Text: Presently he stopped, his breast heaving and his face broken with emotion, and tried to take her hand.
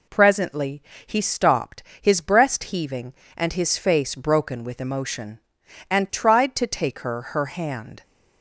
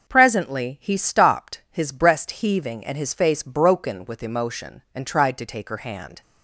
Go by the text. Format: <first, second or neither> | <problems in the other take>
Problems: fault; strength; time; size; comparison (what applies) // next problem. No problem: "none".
second | pauses between "Presently" and "he"; slight; at 0.8 s; 0.24 s long // says "her" twice; at 7.2 s